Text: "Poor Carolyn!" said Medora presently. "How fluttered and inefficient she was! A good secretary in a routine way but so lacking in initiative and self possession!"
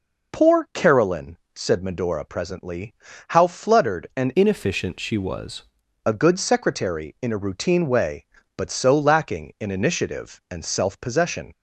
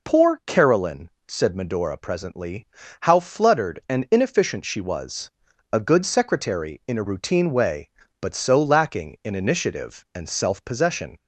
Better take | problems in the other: second | changes voice from "inefficient" to "was"; from 4.3 to 5.6 s; 1.3 s long

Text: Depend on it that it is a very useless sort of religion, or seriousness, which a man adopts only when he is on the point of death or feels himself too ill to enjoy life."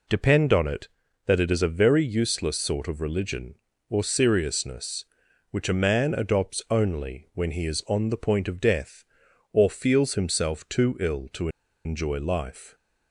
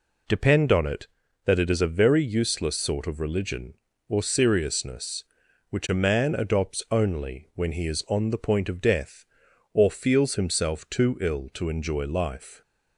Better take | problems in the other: second | pauses between "to" and "enjoy"; at 11.4 s; 0.36 s long

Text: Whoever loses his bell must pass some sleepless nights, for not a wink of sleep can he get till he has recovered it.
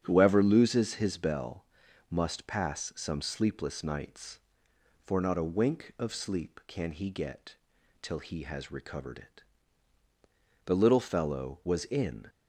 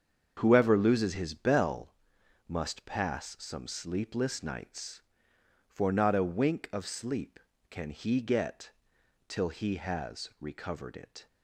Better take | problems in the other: second | starts louder than the rest; strong; until 1.0 s; 8.5 dB; strong in the second // pauses between "bell" and "must"; noticeable; at 1.6 s; 0.46 s long; noticeable in the second // pauses between "get" and "till"; noticeable; at 7.5 s; 0.46 s long; noticeable in the second // goes on to say "The little fellow was in"; from 10.6 s on; 1.6 s long

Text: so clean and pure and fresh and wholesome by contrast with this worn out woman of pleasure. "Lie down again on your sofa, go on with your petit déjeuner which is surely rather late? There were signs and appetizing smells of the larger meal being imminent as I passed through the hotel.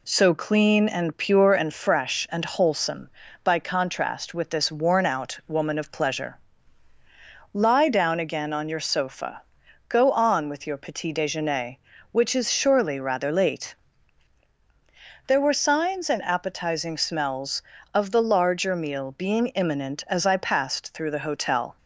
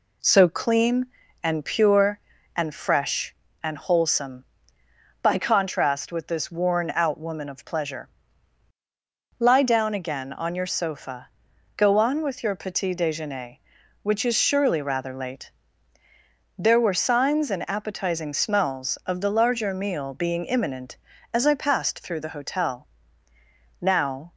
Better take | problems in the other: first | goes on to say "Now"; from 23.7 s on; 0.54 s long

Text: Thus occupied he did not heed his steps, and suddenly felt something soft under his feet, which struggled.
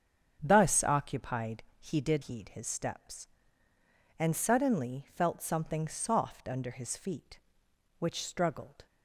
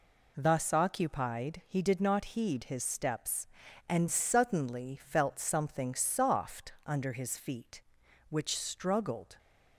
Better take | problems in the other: second | starts louder than the rest; until 1.4 s; 7 dB // pauses between "occupied" and "he"; slight; at 1.6 s; 0.16 s long // skips "not"; at 2.2 s

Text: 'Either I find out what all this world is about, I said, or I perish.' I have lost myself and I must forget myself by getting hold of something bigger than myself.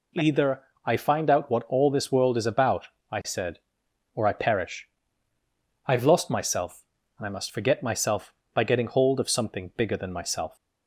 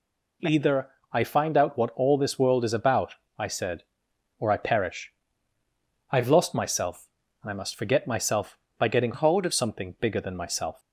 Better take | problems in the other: first | pauses between "Either" and "I"; slight; at 0.8 s; 0.22 s long; slight in the first // changes voice from "hold" to "of"; from 9.1 to 9.5 s; 0.4 s long

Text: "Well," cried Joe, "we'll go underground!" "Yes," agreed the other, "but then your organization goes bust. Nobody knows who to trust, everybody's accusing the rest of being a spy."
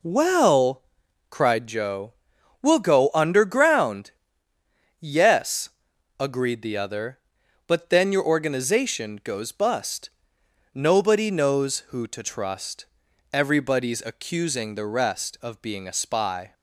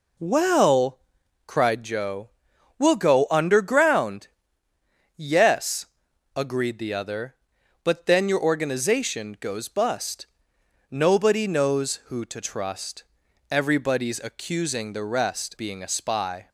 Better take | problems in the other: first | skips "of"; at 15.5 s

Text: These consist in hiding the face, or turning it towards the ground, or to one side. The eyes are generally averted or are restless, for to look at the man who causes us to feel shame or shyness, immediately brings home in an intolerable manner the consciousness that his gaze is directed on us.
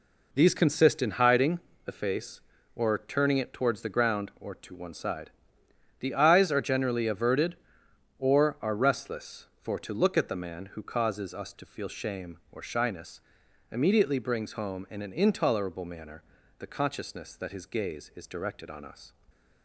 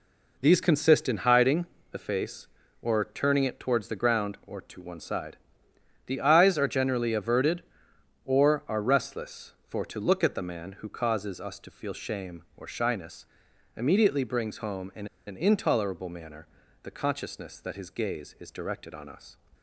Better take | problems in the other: first | pauses between "hiding" and "the"; slight; at 1.6 s; 0.26 s long; slight in the first // pauses between "in" and "an"; slight; at 15.0 s; 0.19 s long // pauses between "manner" and "the"; slight; at 16.4 s; 0.36 s long; slight in the first

